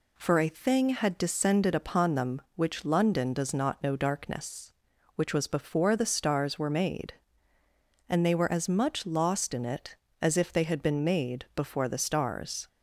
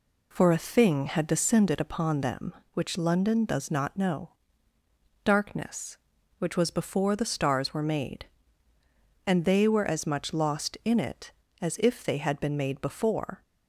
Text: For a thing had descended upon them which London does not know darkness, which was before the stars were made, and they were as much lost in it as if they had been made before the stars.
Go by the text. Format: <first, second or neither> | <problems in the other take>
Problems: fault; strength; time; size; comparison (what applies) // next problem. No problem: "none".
first | pauses between "know" and "darkness"; noticeable; at 4.2 s; 0.94 s long // stops before "the stars"; at 13.4 s